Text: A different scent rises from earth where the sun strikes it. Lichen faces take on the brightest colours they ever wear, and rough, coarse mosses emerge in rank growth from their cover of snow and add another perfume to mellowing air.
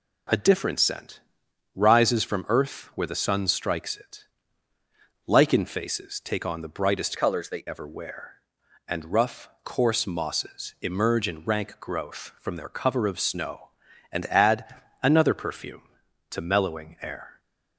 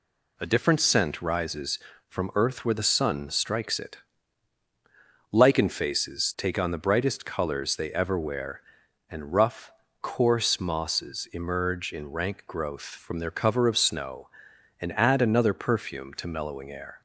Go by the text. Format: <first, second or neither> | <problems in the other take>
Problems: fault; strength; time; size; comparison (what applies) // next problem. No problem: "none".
second | pauses between "scent" and "rises"; noticeable; at 1.2 s; 0.54 s long // changes voice from "colours" to "they"; from 7.1 to 7.6 s; 0.5 s long // pauses between "add" and "another"; slight; at 14.7 s; 0.30 s long